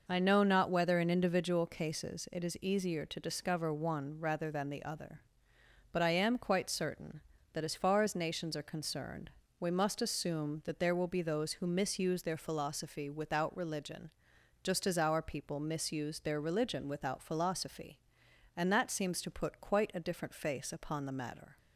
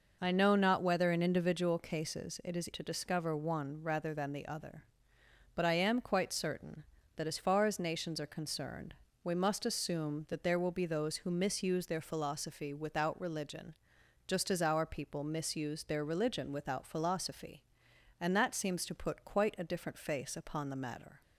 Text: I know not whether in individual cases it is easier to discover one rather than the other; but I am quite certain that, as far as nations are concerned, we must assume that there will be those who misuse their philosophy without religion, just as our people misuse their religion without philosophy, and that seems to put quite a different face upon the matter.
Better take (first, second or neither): first